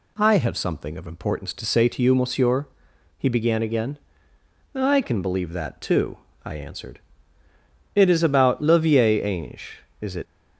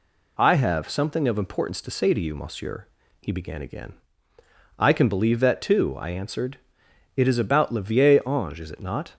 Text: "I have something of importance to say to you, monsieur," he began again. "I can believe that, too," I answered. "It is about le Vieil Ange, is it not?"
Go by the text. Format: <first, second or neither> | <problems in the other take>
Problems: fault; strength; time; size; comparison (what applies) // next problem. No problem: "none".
second | stops before "not"; at 10.2 s